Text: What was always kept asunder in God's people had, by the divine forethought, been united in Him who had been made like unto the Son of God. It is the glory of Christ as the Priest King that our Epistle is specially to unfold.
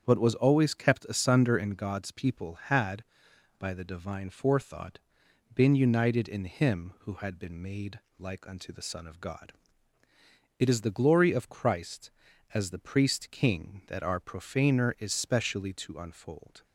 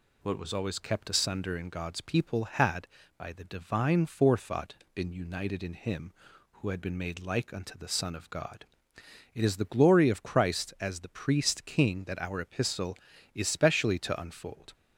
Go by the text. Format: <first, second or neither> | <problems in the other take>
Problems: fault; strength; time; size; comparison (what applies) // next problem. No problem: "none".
second | starts louder than the rest; strong; until 1.0 s; 8 dB // pauses between "made" and "like"; slight; at 7.9 s; 0.20 s long // says "Profaner" for "Epistle"; at 14.1 s